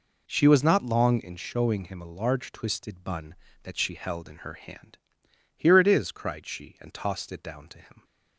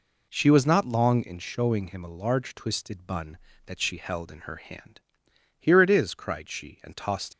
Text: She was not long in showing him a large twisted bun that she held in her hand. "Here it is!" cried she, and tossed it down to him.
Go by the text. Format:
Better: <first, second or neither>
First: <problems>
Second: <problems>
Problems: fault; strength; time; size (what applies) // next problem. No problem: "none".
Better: first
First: none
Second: stops before "it down to him"; at 7.3 s